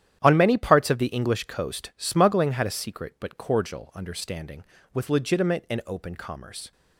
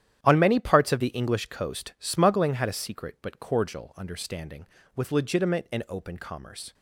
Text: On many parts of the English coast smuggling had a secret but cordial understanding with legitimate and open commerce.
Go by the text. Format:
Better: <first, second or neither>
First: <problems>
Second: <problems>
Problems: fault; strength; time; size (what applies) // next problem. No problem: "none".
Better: neither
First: starts louder than the rest; strong; until 1.2 s; 11 dB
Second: starts louder than the rest; strong; until 1.2 s; 11 dB